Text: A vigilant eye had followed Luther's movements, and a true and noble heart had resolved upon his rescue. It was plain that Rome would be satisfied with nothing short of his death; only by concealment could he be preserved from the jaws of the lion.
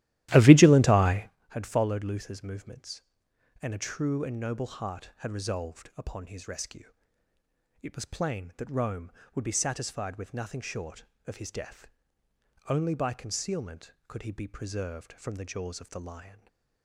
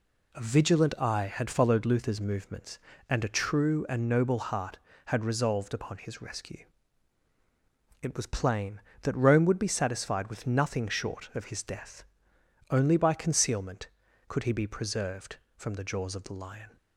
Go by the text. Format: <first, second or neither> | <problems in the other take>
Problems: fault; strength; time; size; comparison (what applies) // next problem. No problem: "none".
second | starts louder than the rest; strong; until 1.4 s; 14.5 dB // stays silent after the last word; slight; from 16.2 s on; 0.6 s long